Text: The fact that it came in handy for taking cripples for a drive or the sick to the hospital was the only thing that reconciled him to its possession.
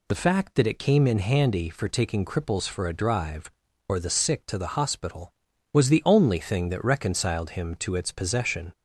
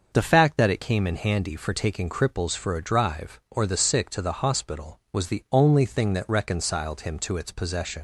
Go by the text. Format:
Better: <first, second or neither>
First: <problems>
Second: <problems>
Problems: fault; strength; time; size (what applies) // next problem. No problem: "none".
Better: first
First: none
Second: starts louder than the rest; until 1.1 s; 6.5 dB // leaves "possession" unfinished; at 7.9 s; 80 ms